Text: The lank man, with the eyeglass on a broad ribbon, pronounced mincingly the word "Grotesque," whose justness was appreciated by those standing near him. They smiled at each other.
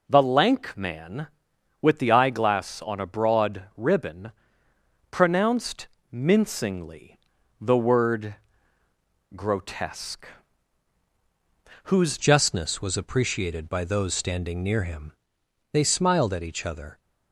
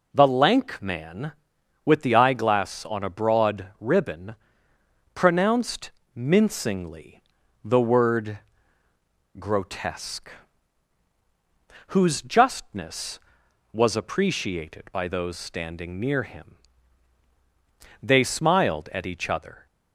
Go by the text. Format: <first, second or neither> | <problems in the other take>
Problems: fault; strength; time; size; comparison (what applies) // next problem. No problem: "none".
second | pauses between "pronounced" and "mincingly"; slight; at 5.8 s; 0.26 s long; slight in the second // pauses between "mincingly" and "the"; at 7.1 s; 0.40 s long; also in the second // pauses between "word" and "Grotesque"; at 8.3 s; 1.0 s long; also in the second // changes voice at "justness"; from 12.1 s on; 4.8 s long